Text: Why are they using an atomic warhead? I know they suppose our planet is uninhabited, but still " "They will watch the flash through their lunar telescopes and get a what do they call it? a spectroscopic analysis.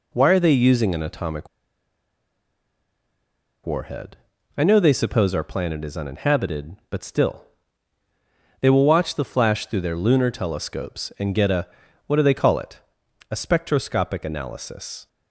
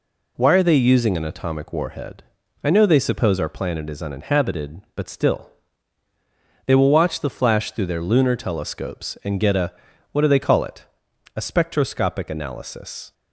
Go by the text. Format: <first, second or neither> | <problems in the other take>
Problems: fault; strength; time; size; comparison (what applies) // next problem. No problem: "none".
second | pauses between "atomic" and "warhead"; strong; at 1.4 s; 2.1 s long // pauses between "a" and "what"; at 11.6 s; 0.38 s long; also in the second